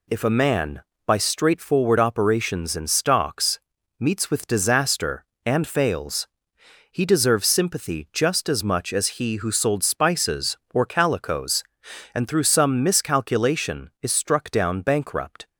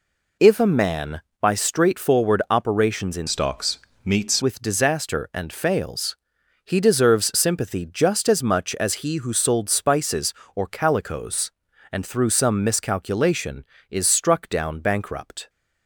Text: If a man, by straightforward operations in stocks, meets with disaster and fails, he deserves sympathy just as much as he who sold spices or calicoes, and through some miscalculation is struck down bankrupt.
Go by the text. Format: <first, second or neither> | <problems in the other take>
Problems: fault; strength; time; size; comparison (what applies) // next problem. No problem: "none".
first | changes voice from "stocks" to "meets"; from 3.2 to 4.4 s; 1.2 s long